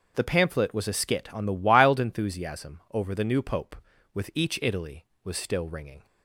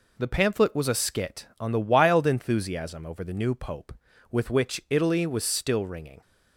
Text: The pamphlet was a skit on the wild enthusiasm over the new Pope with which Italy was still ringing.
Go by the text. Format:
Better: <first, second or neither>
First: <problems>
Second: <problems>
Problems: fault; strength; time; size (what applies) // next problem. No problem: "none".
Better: second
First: starts louder than the rest; until 1.1 s; 6.5 dB // says "each" for "which"; at 4.3 s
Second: none